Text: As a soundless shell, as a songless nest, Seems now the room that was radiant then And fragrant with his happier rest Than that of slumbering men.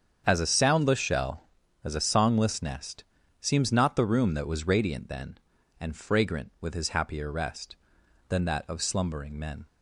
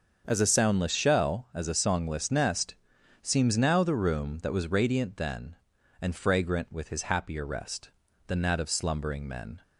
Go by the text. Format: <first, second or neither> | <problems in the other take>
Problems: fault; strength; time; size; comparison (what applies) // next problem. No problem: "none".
second | starts louder than the rest; strong; until 1.2 s; 7.5 dB; also in the second // says "not" for "now"; at 3.7 s